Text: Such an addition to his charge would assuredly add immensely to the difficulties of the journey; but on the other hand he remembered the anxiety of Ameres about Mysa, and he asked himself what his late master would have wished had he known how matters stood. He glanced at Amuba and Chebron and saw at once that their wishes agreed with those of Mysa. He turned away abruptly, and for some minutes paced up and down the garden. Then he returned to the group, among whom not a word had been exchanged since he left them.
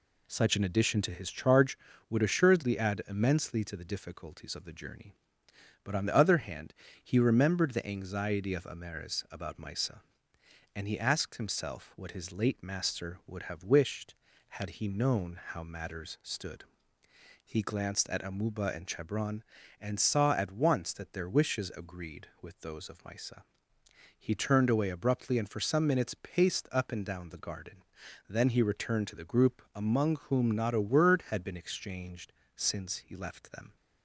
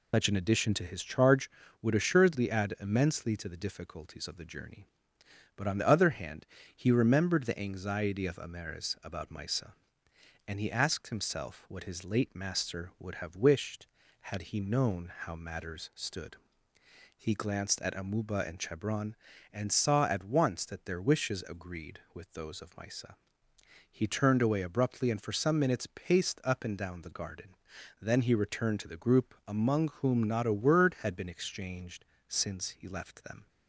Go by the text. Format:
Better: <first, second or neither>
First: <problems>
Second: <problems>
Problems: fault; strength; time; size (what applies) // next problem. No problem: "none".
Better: first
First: pauses between "hand" and "he"; slight; at 6.7 s; 0.28 s long // pauses between "exchanged" and "since"; slight; at 32.3 s; 0.24 s long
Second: loses the start of "Such"; at 0.1 s; 135 ms // pauses between "hand" and "he"; slight; at 6.4 s; 0.28 s long // pauses between "exchanged" and "since"; slight; at 32.0 s; 0.24 s long